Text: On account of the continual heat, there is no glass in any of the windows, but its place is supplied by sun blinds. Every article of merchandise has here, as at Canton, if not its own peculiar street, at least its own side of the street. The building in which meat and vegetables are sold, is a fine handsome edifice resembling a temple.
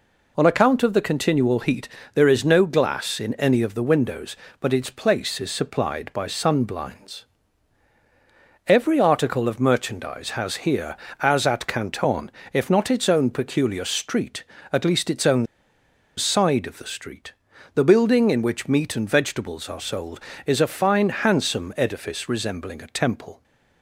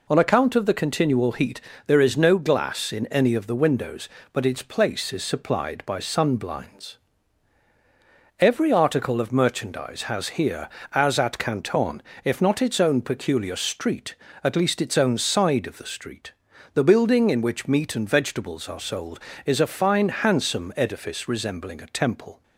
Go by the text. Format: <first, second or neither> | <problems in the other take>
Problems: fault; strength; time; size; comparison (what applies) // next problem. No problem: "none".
second | pauses between "own" and "side"; noticeable; at 15.4 s; 0.71 s long